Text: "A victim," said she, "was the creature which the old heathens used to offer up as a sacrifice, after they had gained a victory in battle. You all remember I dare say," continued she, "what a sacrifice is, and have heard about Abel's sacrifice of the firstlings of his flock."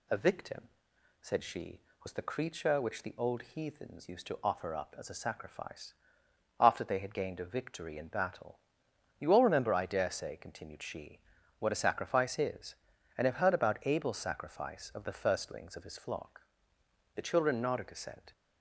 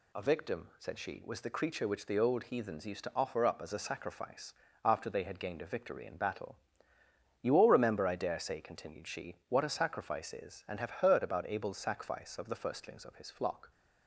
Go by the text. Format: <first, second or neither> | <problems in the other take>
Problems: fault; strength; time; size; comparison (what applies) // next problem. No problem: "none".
second | goes on to say "The children nodded assent"; noticeable; from 17.1 s on; 1.1 s long